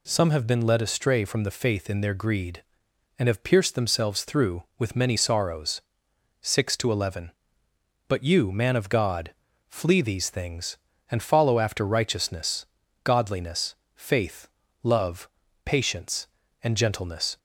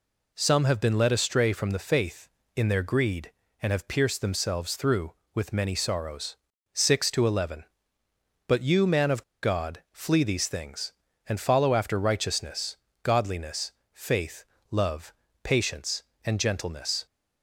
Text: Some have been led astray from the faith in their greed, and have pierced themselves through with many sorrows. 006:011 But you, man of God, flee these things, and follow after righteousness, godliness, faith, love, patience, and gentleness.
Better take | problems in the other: first | pauses between "of" and "God"; slight; at 9.2 s; 0.19 s long

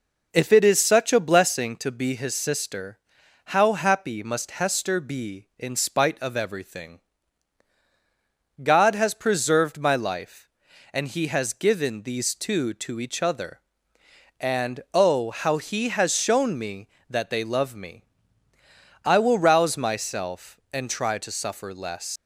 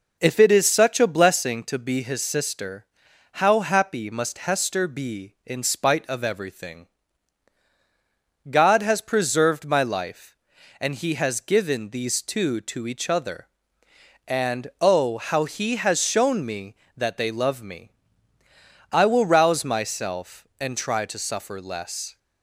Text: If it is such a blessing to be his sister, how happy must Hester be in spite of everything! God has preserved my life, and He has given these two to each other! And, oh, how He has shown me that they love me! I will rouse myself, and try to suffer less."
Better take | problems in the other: second | leaves "less" unfinished; at 22.1 s; 150 ms

